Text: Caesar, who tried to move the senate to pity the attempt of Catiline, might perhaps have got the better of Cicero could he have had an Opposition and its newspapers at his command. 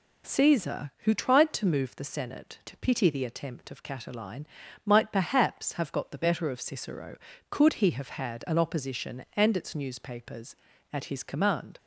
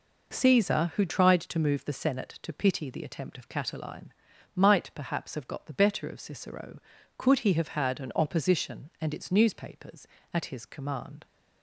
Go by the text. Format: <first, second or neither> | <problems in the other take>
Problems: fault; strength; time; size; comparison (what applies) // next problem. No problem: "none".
neither | none